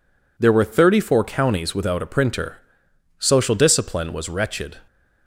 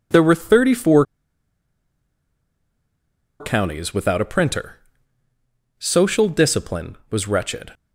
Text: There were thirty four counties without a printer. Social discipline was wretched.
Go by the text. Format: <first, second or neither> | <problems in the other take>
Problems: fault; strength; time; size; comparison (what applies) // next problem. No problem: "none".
first | pauses between "four" and "counties"; strong; at 1.0 s; 2.3 s long